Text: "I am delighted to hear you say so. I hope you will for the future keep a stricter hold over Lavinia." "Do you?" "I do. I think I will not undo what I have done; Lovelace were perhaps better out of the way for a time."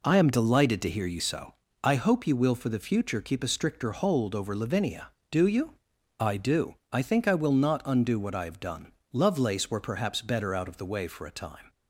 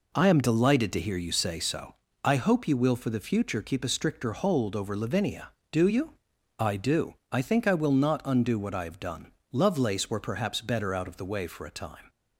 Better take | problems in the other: second | skips "say"; at 1.1 s

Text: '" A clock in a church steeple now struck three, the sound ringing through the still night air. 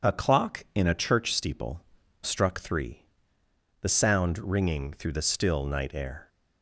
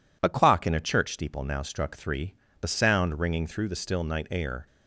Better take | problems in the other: second | skips "now"; at 2.0 s

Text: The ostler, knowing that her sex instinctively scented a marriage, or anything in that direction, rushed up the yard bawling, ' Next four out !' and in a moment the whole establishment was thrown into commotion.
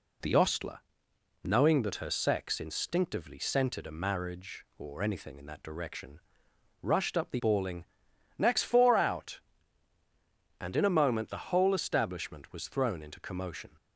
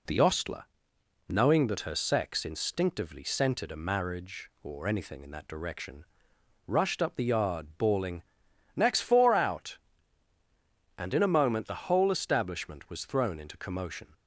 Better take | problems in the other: second | skips "yard"; at 7.3 s

